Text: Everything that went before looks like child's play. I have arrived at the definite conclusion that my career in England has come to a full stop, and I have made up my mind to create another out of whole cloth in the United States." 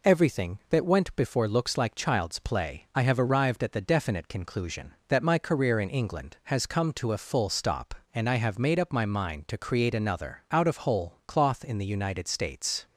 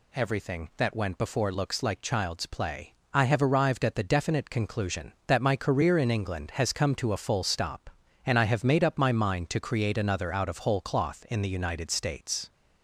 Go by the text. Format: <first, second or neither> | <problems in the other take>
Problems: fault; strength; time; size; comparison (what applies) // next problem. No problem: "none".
neither | none